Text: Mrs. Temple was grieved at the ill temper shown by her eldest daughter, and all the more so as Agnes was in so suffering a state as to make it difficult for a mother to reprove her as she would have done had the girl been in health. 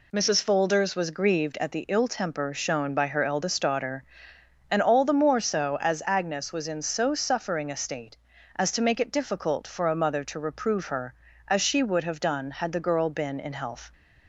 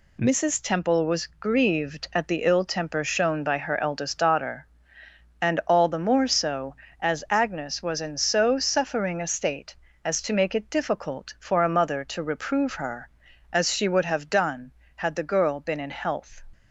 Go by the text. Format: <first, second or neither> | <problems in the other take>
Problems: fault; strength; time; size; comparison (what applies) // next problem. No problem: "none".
second | says "Folders" for "Temple"; at 0.4 s